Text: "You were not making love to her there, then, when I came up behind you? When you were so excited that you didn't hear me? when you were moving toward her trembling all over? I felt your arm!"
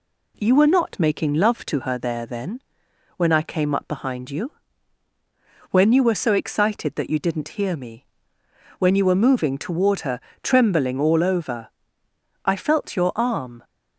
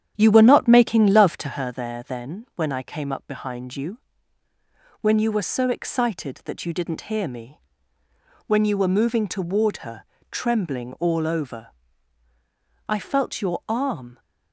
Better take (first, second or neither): first